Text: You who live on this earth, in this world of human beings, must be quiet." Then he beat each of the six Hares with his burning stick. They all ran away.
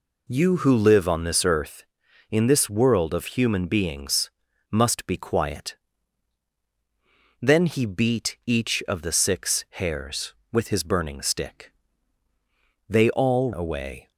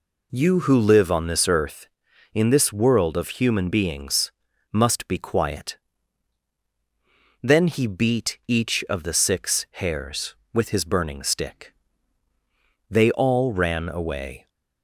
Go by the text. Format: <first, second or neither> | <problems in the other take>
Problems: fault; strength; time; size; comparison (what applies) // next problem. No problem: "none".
second | skips "ran"; at 13.5 s